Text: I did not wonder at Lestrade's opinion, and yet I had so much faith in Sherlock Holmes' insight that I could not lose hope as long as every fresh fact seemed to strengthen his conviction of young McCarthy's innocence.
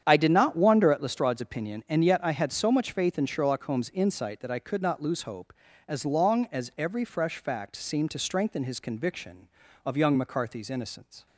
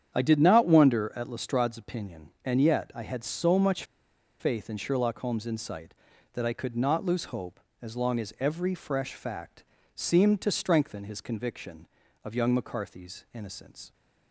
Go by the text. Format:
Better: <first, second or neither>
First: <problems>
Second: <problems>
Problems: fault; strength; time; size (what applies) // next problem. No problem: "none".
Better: first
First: starts louder than the rest; strong; until 1.0 s; 9 dB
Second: starts louder than the rest; strong; until 1.1 s; 8.5 dB // pauses between "much" and "faith"; noticeable; at 3.8 s; 0.57 s long // pauses between "fact" and "seemed"; slight; at 9.6 s; 0.32 s long